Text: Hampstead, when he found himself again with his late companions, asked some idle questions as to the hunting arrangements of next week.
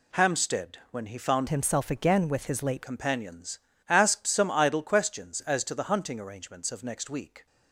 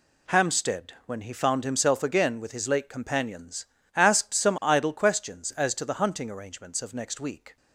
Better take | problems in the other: second | changes voice from "himself" to "late"; from 1.4 to 2.8 s; 1.4 s long

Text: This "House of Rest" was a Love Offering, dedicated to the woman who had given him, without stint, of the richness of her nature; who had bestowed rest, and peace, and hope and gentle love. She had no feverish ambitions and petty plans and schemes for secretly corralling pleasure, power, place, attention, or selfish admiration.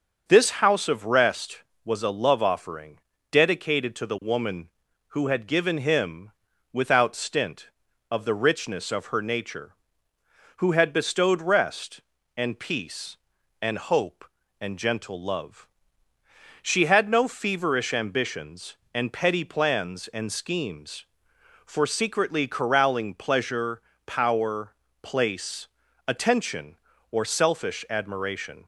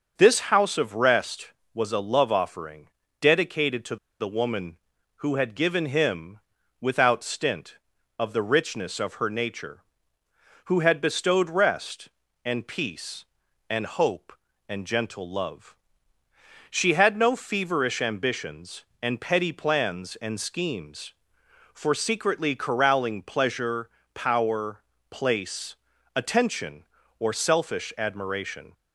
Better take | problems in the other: first | starts louder than the rest; until 1.1 s; 6.5 dB; also in the first // pauses between "to" and "the"; slight; at 3.9 s; 0.24 s long

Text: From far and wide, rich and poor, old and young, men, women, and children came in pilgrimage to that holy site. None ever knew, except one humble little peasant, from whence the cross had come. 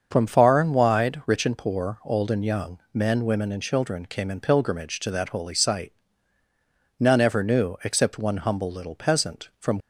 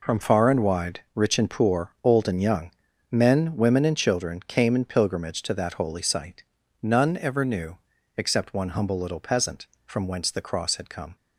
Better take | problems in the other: second | starts louder than the rest; until 1.1 s; 6.5 dB // stops before "whence the cross had come"; at 9.7 s

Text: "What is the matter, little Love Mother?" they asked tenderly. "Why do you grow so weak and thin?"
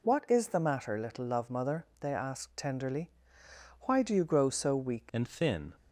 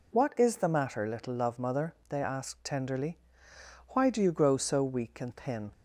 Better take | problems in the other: second | changes voice at "and"; from 5.1 s on; 0.6 s long

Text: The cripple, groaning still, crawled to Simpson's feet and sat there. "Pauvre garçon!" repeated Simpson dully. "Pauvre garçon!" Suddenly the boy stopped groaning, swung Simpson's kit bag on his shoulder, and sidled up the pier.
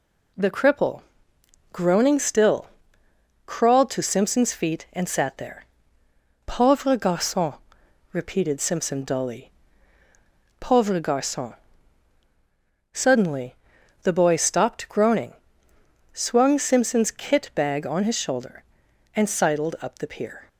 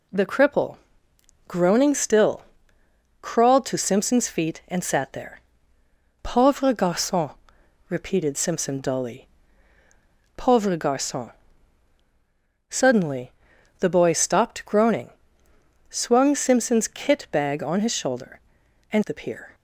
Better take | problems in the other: first | pauses between "Suddenly" and "the"; noticeable; at 13.3 s; 0.48 s long; noticeable in the first // skips "sidled up"; at 19.0 s

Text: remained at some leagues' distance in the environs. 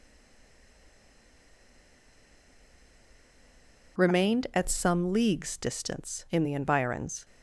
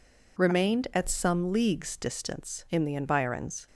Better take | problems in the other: second | stays silent before the first word; strong; until 3.9 s; 3.9 s long

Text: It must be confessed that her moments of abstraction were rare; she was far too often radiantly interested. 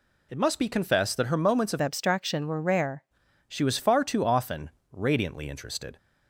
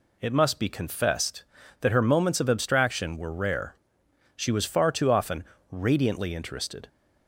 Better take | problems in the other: second | changes voice from "abstraction" to "rare"; from 1.8 to 3.0 s; 1.2 s long // pauses between "often" and "radiantly"; slight; at 4.6 s; 0.24 s long; slight in the second

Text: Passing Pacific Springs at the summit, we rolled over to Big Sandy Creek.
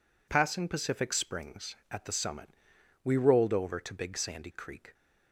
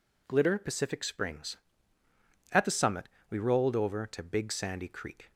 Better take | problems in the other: first | says "Glitter" for "Passing"; at 0.2 s

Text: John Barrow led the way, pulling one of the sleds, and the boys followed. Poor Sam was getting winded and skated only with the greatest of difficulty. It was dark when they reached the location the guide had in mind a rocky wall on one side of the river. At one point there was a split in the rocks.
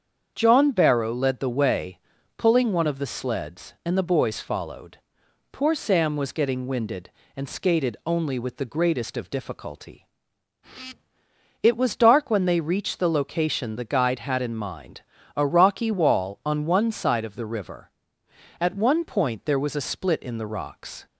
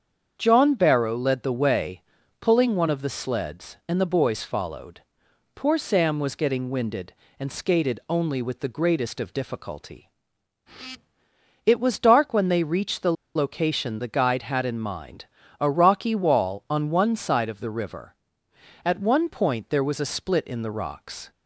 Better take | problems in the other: first | starts louder than the rest; strong; until 1.3 s; 7.5 dB; strong in the first // pauses between "the" and "location"; slight; at 13.1 s; 0.23 s long // pauses between "mind" and "a"; slight; at 15.2 s; 0.34 s long; slight in the first

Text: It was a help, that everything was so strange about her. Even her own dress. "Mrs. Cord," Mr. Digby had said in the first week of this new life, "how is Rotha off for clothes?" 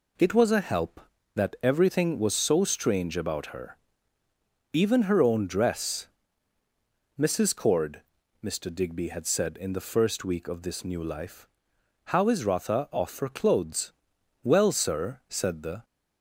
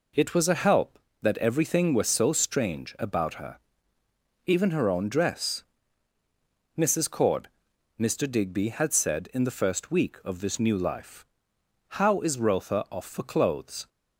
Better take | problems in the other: second | goes on to say "Well sir said the"; from 14.4 s on; 1.4 s long

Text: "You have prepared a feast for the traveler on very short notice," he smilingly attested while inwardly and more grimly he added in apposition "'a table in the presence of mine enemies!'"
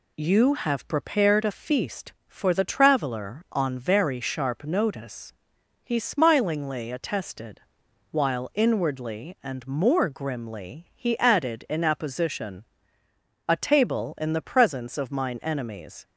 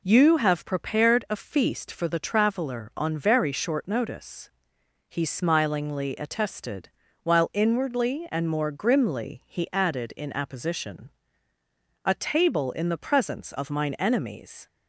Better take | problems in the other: second | says "sharp" for "short"; at 4.2 s // pauses between "attested" and "while"; noticeable; at 7.6 s; 0.50 s long; slight in the second // pauses between "apposition" and "a"; noticeable; at 12.6 s; 0.84 s long; noticeable in the second

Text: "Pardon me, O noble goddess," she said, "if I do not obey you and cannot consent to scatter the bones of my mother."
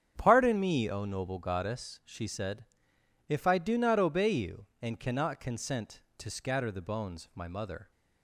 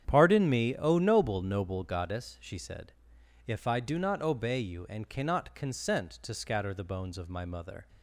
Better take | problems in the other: first | starts louder than the rest; strong; until 1.0 s; 8.5 dB; strong in the first // says "noble" twice; at 1.4 s

